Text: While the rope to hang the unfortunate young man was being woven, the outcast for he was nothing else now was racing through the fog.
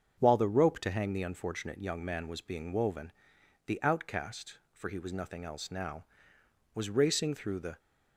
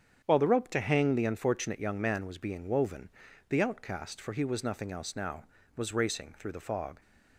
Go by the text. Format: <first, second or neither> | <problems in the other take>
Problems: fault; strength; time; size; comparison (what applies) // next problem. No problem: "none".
second | starts louder than the rest; until 1.1 s; 7 dB; strong in the second // stops before "fog"; at 7.7 s